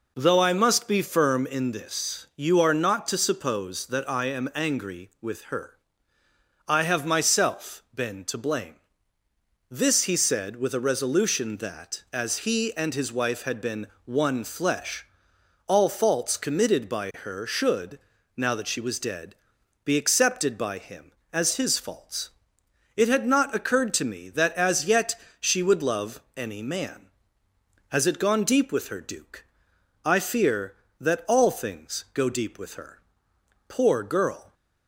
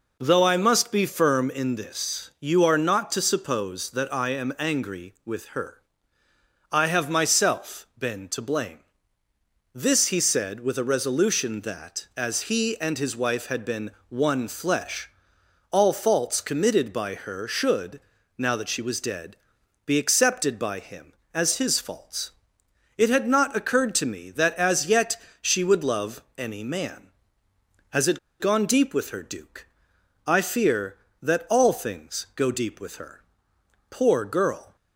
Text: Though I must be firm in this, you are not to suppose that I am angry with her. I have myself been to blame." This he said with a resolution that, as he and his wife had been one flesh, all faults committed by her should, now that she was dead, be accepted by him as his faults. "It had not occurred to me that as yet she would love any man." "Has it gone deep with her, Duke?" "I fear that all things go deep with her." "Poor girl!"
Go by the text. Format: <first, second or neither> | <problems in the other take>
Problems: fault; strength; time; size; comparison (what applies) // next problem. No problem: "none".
first | pauses between "been" and "one"; slight; at 13.9 s; 0.18 s long; slight in the first // pauses between "yet" and "she"; slight; at 25.1 s; 0.26 s long; slight in the first // pauses between "it" and "gone"; slight; at 28.1 s; 0.21 s long